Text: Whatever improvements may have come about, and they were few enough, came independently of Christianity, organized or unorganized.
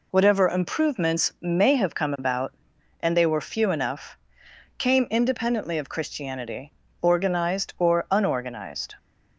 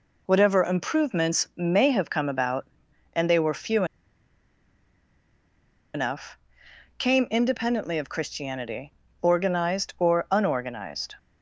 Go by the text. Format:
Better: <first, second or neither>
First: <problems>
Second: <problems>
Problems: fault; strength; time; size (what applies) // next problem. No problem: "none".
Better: first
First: none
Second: pauses between "few" and "enough"; strong; at 3.8 s; 2.0 s long